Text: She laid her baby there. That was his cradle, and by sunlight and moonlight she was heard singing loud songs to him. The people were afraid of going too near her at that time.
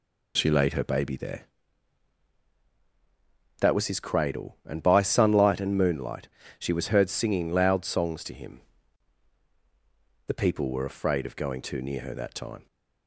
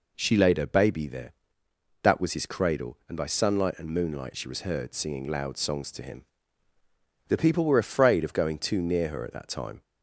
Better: second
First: pauses between "moonlight" and "she"; slight; at 6.2 s; 0.30 s long // skips "at"; at 12.1 s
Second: none

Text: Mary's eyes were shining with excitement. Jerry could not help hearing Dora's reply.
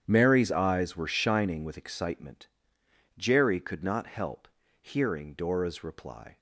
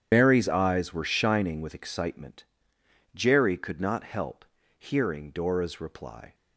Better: first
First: starts louder than the rest; strong; until 1.0 s; 9 dB // pauses between "help" and "hearing"; slight; at 4.4 s; 0.32 s long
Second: loses the start of "Mary's"; at 0.1 s; 80 ms // starts louder than the rest; strong; until 1.1 s; 9 dB // pauses between "help" and "hearing"; slight; at 4.4 s; 0.32 s long

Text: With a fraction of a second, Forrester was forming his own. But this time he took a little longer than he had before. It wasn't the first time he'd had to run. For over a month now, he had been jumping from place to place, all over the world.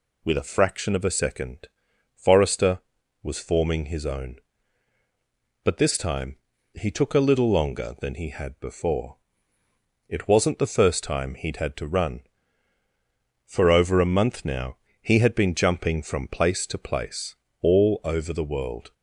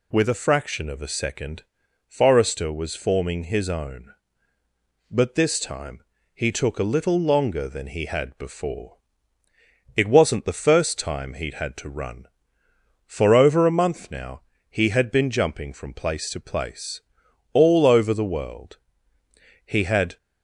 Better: first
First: pauses between "time" and "he"; slight; at 6.3 s; 0.36 s long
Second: pauses between "time" and "he"; slight; at 6.0 s; 0.34 s long // goes on to say "He had"; from 19.6 s on; 0.52 s long

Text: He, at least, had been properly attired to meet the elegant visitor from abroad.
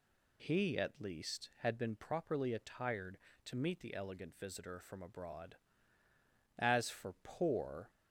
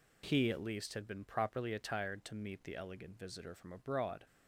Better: second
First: goes on to say "As for poor"; from 6.5 s on; 1.3 s long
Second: none

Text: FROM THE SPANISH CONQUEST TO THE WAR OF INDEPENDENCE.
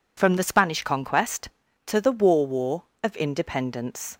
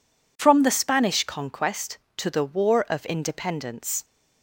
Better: second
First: says "WAR" twice; at 2.4 s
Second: none

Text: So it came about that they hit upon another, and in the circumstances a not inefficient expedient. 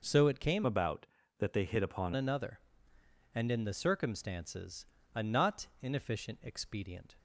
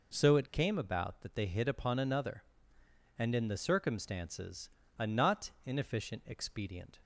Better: second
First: changes voice from "about" to "upon"; from 0.6 to 2.1 s; 1.5 s long // pauses between "circumstances" and "a"; slight; at 4.8 s; 0.28 s long // pauses between "not" and "inefficient"; slight; at 5.6 s; 0.16 s long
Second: pauses between "circumstances" and "a"; slight; at 4.6 s; 0.28 s long // pauses between "not" and "inefficient"; slight; at 5.4 s; 0.16 s long

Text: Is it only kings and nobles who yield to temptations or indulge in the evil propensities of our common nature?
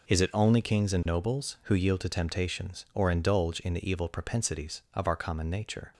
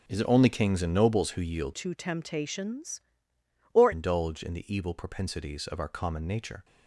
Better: first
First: none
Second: changes voice from "to" to "or"; from 1.7 to 3.9 s; 2.2 s long

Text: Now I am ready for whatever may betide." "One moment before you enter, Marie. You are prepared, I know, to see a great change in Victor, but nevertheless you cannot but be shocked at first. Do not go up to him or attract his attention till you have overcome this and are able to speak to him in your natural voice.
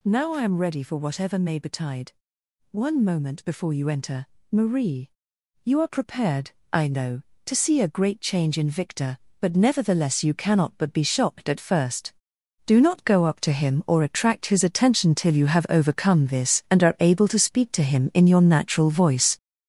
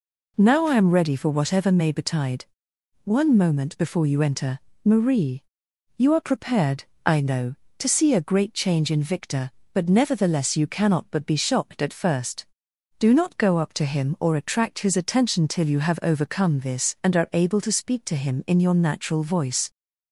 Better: second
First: gets louder; strong; throughout; 7.5 dB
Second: none

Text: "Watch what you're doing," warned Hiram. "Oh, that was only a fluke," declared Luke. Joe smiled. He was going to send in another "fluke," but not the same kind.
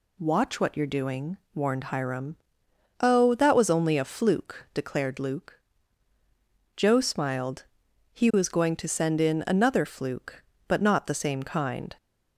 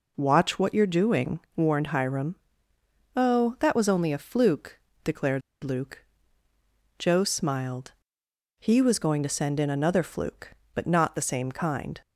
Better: first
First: none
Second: pauses between "declared" and "Luke"; slight; at 5.4 s; 0.21 s long

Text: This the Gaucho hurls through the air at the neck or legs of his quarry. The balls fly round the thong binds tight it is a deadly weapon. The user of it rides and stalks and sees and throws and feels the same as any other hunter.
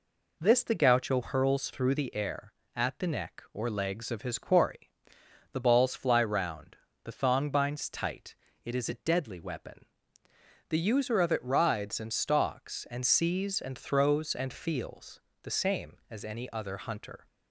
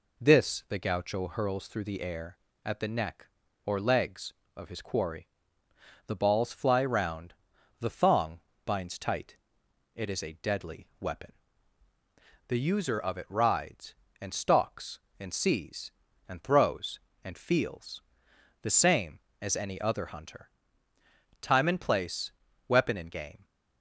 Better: first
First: pauses between "round" and "the"; slight; at 6.7 s; 0.26 s long // pauses between "tight" and "it"; slight; at 8.3 s; 0.26 s long // pauses between "feels" and "the"; slight; at 15.2 s; 0.20 s long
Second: pauses between "round" and "the"; noticeable; at 7.3 s; 0.46 s long // pauses between "thong" and "binds"; slight; at 8.3 s; 0.24 s long // pauses between "tight" and "it"; noticeable; at 9.3 s; 0.59 s long // pauses between "feels" and "the"; noticeable; at 18.0 s; 0.62 s long // goes on to say "Time and place weapon and game"; strong; from 21.4 s on; 2.0 s long

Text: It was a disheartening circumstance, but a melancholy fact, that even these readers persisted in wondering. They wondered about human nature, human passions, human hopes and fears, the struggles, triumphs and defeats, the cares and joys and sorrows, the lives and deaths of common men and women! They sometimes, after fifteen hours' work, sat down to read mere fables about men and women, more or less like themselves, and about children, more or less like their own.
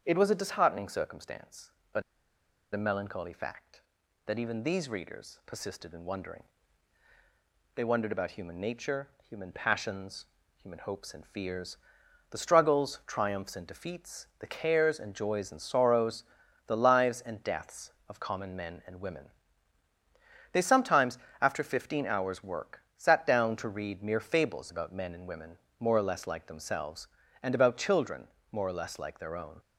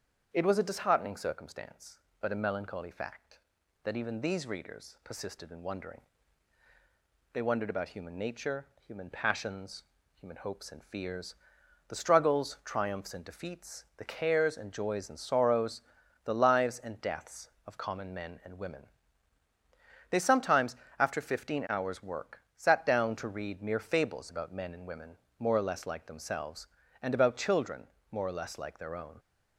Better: second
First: starts louder than the rest; strong; until 1.0 s; 7.5 dB // pauses between "but" and "a"; noticeable; at 2.0 s; 0.71 s long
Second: starts louder than the rest; strong; until 1.3 s; 7.5 dB

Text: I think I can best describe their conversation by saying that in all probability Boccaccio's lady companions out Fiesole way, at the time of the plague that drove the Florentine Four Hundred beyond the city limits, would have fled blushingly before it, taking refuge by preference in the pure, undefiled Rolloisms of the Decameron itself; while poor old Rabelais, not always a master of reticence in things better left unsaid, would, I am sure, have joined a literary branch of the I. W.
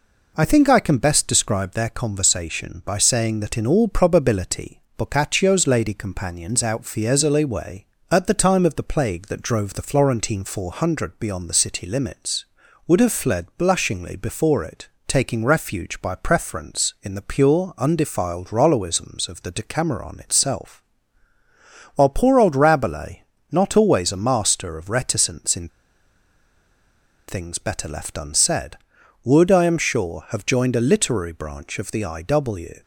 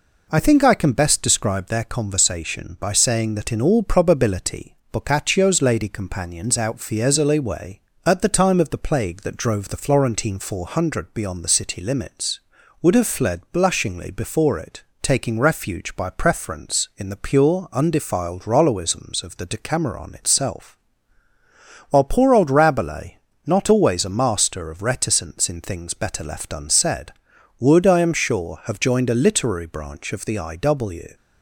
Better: second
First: pauses between "probability" and "Boccaccio's"; slight; at 4.8 s; 0.16 s long // pauses between "in" and "things"; strong; at 25.6 s; 1.5 s long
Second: pauses between "probability" and "Boccaccio's"; slight; at 4.7 s; 0.16 s long

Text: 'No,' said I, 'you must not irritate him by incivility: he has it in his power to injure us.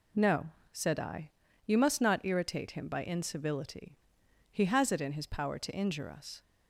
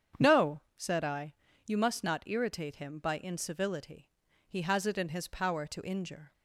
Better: first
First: none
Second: starts louder than the rest; strong; until 1.3 s; 8 dB // stops before "us"; at 6.3 s

